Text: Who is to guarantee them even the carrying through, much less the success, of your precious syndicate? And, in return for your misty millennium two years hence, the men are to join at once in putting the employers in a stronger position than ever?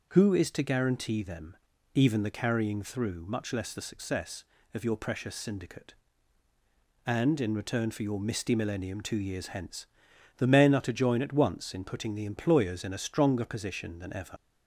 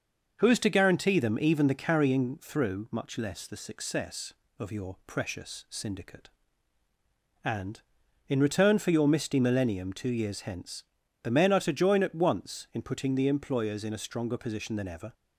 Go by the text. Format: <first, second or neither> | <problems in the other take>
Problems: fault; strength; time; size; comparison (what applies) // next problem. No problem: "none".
second | pauses between "them" and "even"; slight; at 1.5 s; 0.36 s long // leaves "ever" unfinished; at 14.3 s; 60 ms